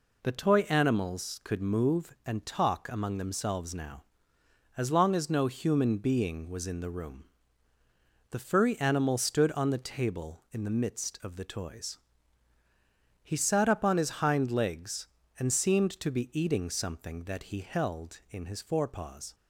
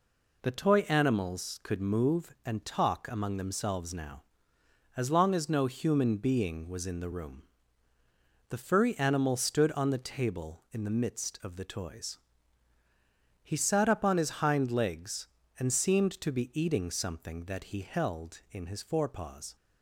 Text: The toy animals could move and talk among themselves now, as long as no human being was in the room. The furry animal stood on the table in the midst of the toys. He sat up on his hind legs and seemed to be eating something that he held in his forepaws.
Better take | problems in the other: neither | none

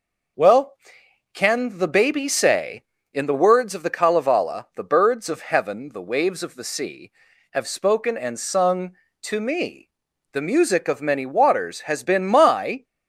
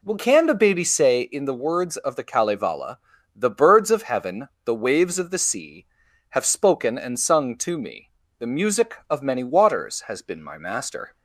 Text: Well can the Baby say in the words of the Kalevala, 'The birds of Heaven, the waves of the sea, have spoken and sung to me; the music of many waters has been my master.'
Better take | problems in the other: second | stops before "master"; at 12.8 s

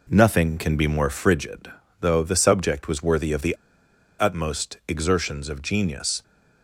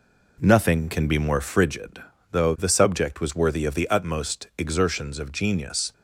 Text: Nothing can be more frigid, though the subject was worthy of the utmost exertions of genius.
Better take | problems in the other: second | pauses between "the" and "utmost"; noticeable; at 3.5 s; 0.65 s long

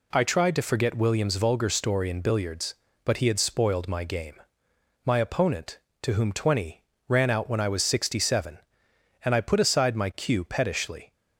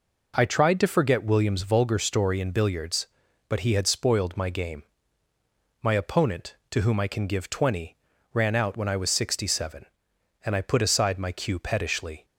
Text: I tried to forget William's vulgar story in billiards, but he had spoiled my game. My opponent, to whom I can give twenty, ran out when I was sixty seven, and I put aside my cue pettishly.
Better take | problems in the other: second | skips "I can give"; at 6.3 s

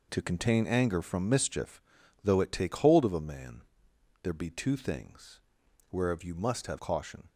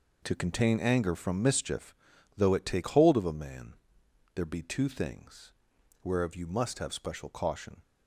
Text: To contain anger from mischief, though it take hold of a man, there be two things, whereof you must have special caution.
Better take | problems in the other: second | skips "special"; at 6.7 s

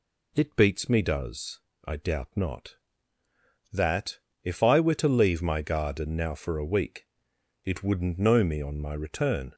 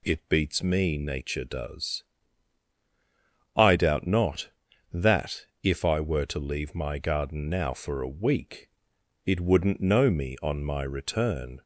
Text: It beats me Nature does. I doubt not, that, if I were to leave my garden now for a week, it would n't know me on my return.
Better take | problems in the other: second | skips "Nature"; at 1.0 s

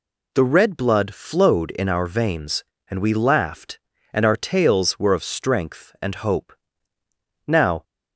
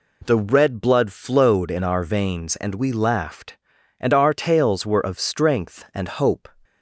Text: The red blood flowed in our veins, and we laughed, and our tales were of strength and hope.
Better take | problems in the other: second | goes on to say "Now"; slight; from 7.4 s on; 0.36 s long

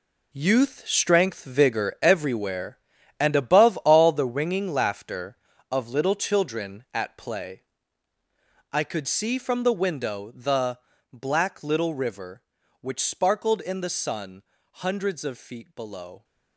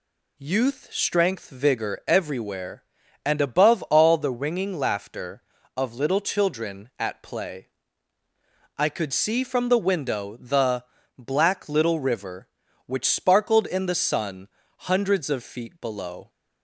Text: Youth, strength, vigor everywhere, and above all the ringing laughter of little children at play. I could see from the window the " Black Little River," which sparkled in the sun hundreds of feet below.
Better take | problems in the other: second | gets quieter; strong; throughout; 11.5 dB // pauses between "sun" and "hundreds"; slight; at 14.4 s; 0.34 s long; slight in the second

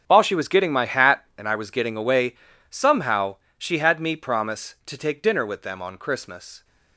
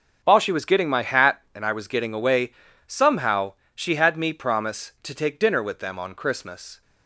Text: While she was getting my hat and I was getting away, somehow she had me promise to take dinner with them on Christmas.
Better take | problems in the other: second | gets quieter; strong; throughout; 14 dB // starts louder than the rest; strong; until 1.0 s; 7.5 dB; also in the second // pauses between "somehow" and "she"; slight; at 3.3 s; 0.22 s long; slight in the second

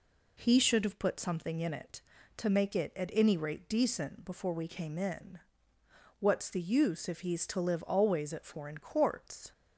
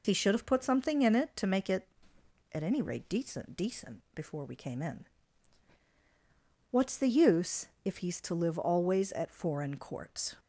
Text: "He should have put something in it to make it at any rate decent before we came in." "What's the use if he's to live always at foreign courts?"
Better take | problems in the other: first | says "decent" twice; at 3.5 s // pauses between "use" and "if"; slight; at 7.6 s; 0.18 s long

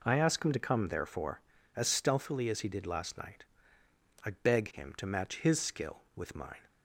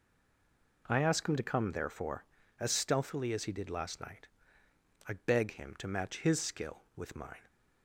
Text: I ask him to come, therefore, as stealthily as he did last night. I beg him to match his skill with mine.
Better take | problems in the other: first | stays silent before the first word; slight; until 0.8 s; 0.8 s long

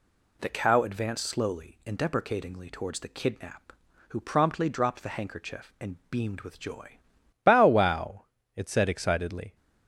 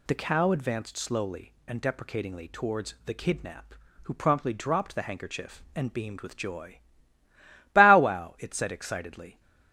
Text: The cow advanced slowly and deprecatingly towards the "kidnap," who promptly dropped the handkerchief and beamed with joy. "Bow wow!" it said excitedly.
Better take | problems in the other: second | changes voice at "Bow"; from 7.4 s on; 2.1 s long

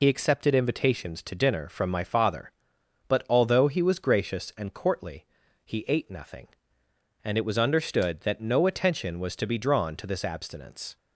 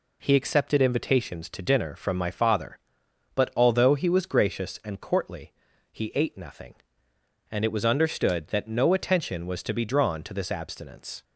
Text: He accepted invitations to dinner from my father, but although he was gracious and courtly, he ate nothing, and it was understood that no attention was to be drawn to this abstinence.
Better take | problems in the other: second | loses the start of "He"; at 0.0 s; 70 ms

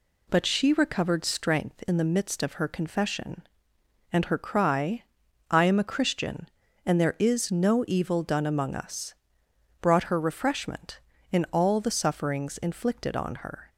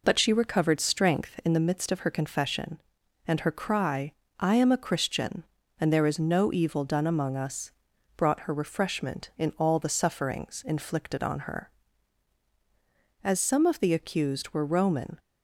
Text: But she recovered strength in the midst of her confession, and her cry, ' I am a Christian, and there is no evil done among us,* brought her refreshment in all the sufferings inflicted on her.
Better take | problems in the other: first | goes on to say "As some of the accused were Roman"; strong; from 13.2 s on; 1.9 s long

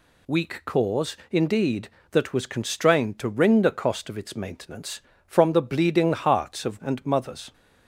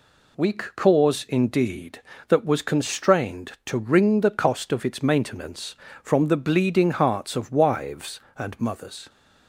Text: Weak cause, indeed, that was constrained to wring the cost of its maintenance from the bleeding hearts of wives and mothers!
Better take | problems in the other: second | skips "wives"; at 6.8 s

